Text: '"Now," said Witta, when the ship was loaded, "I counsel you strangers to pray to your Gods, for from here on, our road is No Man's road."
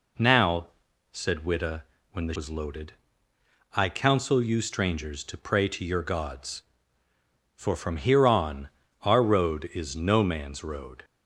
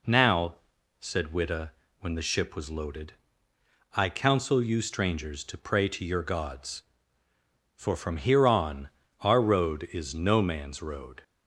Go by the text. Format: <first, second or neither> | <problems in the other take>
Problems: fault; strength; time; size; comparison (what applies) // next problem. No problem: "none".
second | skips "ship"; at 2.3 s